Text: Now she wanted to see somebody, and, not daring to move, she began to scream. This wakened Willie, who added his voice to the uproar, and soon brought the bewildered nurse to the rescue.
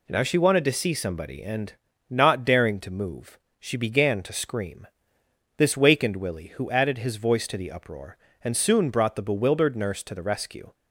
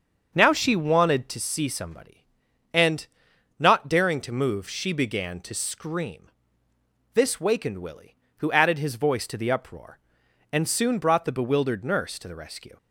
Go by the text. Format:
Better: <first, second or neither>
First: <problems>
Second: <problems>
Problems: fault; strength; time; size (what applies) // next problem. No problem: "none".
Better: first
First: none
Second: starts louder than the rest; until 1.4 s; 6.5 dB